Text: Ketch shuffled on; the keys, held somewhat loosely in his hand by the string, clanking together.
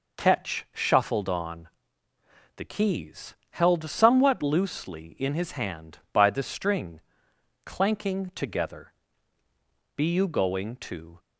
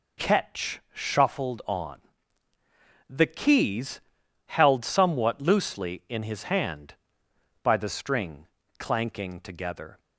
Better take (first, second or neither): second